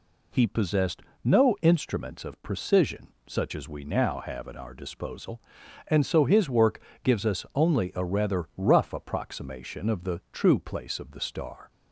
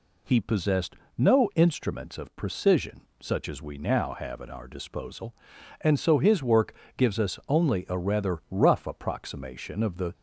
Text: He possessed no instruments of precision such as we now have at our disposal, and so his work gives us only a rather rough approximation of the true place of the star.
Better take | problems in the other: first | pauses between "possessed" and "no"; slight; at 0.9 s; 0.22 s long; slight in the first // pauses between "precision" and "such"; slight; at 3.0 s; 0.20 s long; slight in the first // pauses between "work" and "gives"; slight; at 6.7 s; 0.24 s long; slight in the first // stops before "true place of the star"; at 10.1 s

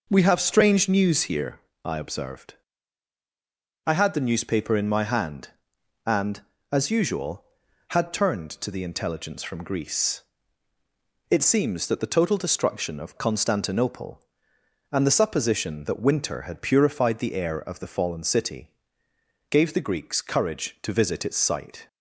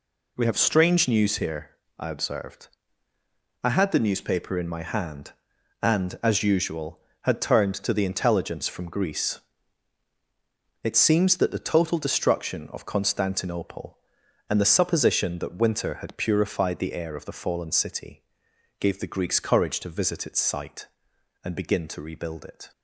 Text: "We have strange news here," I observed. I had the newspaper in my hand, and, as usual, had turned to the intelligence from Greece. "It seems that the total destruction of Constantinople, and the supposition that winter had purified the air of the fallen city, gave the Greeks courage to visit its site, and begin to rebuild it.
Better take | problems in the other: second | stops before "and begin to rebuild it"; at 21.8 s

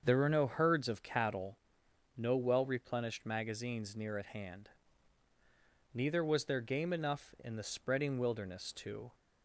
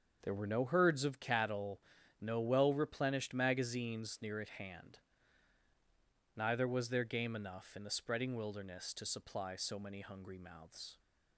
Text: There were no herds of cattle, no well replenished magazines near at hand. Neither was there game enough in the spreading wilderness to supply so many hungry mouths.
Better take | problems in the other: second | starts louder than the rest; until 1.0 s; 7 dB; also in the second // stops before "supply so many hungry mouths"; at 9.1 s

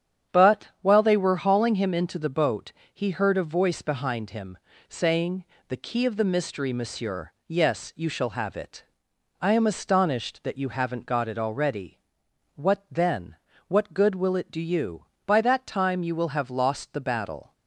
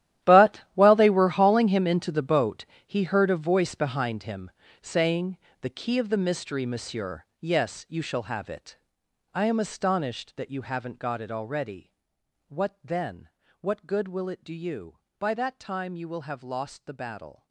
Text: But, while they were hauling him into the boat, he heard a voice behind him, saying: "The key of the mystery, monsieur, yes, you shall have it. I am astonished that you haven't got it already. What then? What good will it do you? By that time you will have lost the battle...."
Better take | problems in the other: first | gets quieter; strong; throughout; 17 dB // starts louder than the rest; strong; until 1.3 s; 13 dB; strong in the first

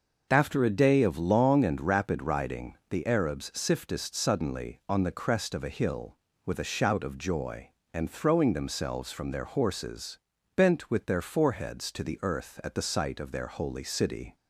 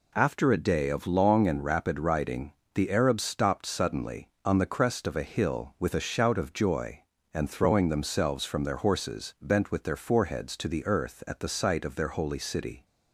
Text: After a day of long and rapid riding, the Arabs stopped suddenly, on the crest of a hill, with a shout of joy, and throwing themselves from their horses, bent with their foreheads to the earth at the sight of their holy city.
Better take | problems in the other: second | says "siftest" for "stopped"; at 3.5 s

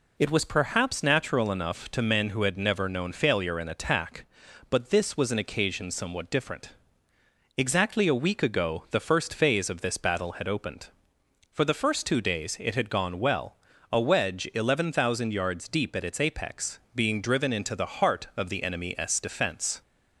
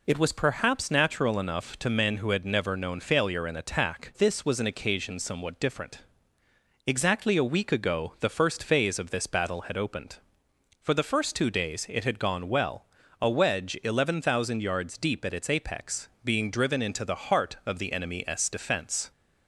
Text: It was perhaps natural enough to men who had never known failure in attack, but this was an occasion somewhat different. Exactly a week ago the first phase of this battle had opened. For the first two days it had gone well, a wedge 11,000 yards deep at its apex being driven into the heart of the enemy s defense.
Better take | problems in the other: first | skips "but"; at 4.1 s

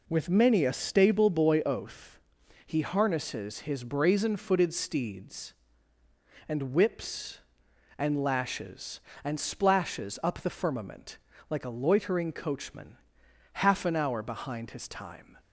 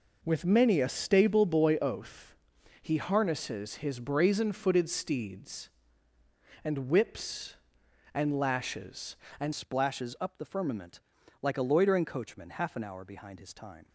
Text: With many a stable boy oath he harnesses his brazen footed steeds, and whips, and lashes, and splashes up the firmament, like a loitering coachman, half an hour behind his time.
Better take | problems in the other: first | pauses between "oath" and "he"; at 2.3 s; 0.44 s long; also in the first // changes voice at "splashes"; from 9.5 s on; 4.3 s long

